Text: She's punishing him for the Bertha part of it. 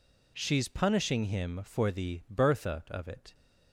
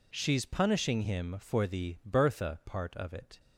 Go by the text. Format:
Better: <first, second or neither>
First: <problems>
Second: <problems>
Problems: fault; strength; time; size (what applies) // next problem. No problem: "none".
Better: second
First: skips "part"; at 2.8 s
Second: none